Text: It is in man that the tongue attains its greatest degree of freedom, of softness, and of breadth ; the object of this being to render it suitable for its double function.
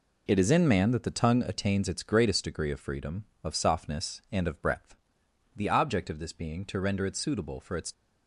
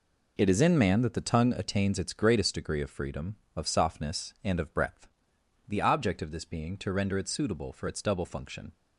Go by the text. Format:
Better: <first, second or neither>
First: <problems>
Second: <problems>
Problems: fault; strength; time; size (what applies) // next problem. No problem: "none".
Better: second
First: stops before "double function"; at 7.9 s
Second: none